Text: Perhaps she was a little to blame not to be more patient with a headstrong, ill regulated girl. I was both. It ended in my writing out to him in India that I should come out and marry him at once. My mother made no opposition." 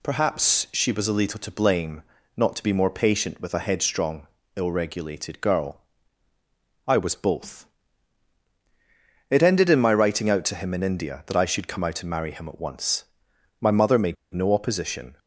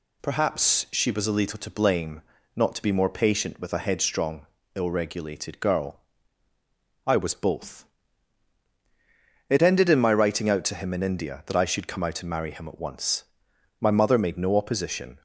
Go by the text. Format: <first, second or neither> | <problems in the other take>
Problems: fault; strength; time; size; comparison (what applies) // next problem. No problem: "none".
second | pauses between "blame" and "not"; slight; at 2.0 s; 0.34 s long; slight in the second // pauses between "made" and "no"; slight; at 14.1 s; 0.18 s long